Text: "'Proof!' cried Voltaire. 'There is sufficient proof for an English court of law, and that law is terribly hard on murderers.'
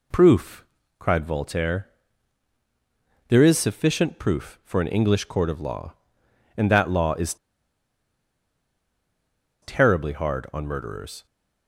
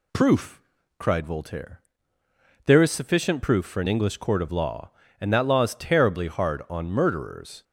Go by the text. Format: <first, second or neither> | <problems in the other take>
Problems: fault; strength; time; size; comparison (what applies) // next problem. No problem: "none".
second | pauses between "is" and "terribly"; strong; at 7.3 s; 2.2 s long